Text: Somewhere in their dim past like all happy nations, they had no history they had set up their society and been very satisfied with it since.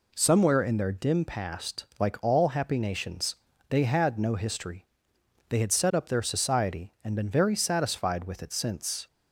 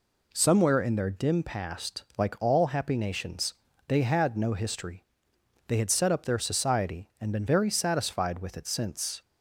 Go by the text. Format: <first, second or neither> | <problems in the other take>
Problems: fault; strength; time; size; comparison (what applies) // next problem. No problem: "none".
neither | pauses between "history" and "they"; noticeable; the same in both